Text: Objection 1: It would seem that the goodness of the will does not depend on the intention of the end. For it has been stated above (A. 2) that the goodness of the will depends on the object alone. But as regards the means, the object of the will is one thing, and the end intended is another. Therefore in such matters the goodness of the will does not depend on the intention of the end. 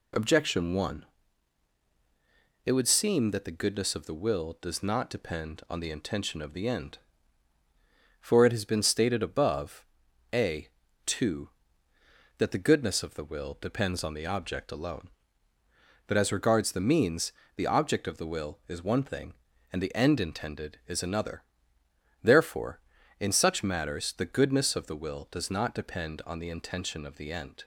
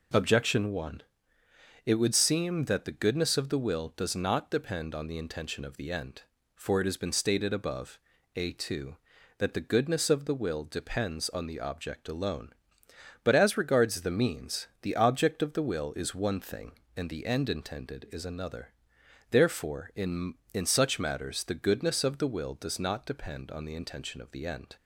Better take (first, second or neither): first